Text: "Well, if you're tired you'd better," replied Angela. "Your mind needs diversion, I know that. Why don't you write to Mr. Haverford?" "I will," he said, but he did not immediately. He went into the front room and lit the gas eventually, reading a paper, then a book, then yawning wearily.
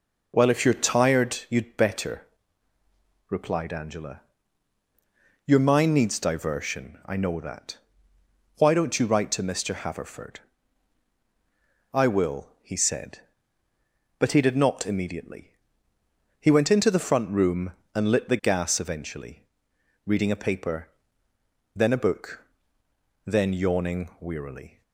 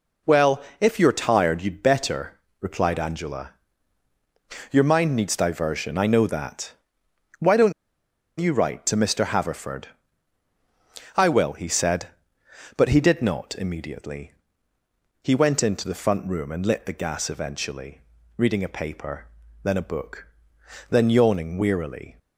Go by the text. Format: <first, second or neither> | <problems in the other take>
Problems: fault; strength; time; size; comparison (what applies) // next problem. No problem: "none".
first | pauses between "don't" and "you"; noticeable; at 7.7 s; 0.67 s long